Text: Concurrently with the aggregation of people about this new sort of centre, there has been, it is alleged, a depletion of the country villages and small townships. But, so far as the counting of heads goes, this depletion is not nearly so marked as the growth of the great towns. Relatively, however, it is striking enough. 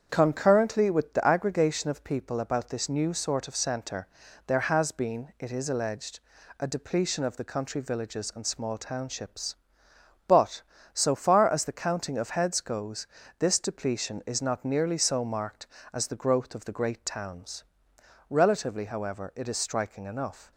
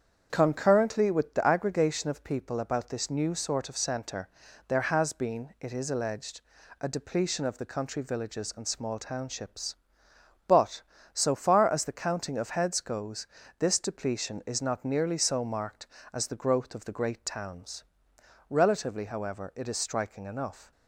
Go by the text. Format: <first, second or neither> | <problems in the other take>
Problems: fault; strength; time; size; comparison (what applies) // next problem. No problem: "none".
neither | starts louder than the rest; strong; the same in both